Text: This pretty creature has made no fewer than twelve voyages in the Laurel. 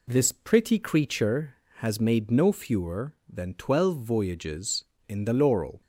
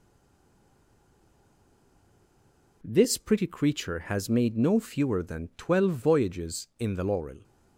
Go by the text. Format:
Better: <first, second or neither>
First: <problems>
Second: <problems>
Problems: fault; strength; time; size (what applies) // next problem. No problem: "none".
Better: first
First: none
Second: stays silent before the first word; strong; until 2.8 s; 2.8 s long